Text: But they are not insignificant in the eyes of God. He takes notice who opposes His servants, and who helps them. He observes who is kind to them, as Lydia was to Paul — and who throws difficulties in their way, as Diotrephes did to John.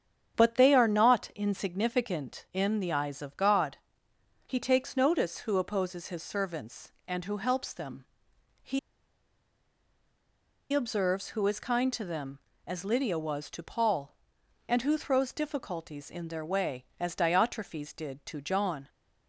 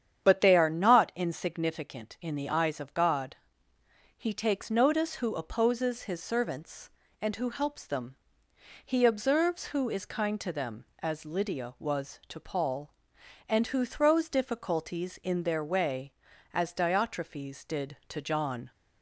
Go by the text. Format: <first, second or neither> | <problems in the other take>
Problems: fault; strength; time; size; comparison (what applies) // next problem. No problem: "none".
second | starts louder than the rest; strong; until 1.4 s; 8 dB; strong in the second // pauses between "He" and "observes"; strong; at 8.7 s; 1.9 s long